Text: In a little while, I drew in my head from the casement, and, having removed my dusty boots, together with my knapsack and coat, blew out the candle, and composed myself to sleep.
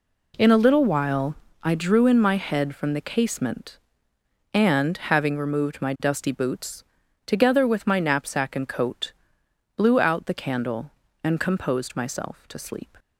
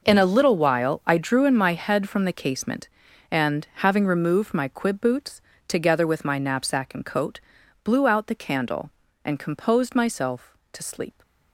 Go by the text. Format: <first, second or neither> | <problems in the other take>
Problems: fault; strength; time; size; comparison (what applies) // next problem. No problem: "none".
first | says "quib" for "dusty"; at 4.6 s